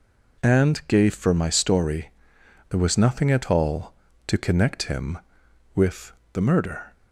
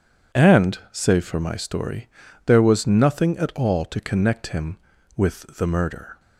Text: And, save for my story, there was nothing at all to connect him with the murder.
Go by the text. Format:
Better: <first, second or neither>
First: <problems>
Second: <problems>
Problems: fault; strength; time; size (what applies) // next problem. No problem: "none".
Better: second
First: says "gave" for "save"; at 0.8 s // pauses between "with" and "the"; slight; at 6.1 s; 0.20 s long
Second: none